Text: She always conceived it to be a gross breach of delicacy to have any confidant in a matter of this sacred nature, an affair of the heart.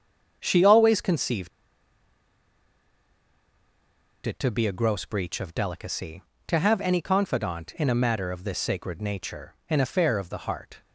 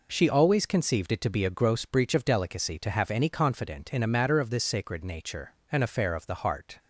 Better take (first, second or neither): second